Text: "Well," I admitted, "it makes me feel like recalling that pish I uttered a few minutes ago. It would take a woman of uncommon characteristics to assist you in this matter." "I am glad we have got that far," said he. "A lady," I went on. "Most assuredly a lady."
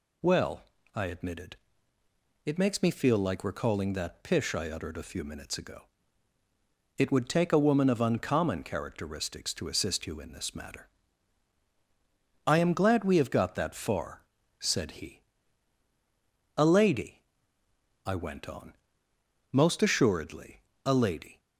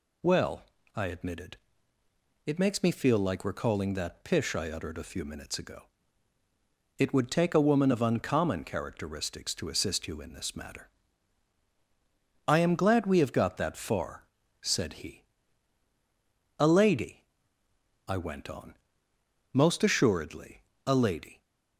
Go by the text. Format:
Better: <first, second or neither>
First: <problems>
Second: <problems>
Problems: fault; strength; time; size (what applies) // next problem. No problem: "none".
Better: neither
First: pauses between "assuredly" and "a"; slight; at 20.6 s; 0.22 s long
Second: pauses between "assuredly" and "a"; slight; at 20.6 s; 0.22 s long